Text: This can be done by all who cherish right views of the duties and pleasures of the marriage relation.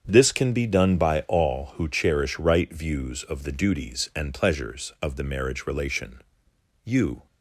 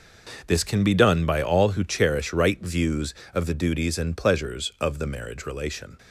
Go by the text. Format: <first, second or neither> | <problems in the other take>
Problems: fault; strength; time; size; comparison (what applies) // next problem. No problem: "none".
second | starts louder than the rest; strong; until 1.0 s; 7.5 dB // goes on to say "You"; slight; from 6.8 s on; 0.42 s long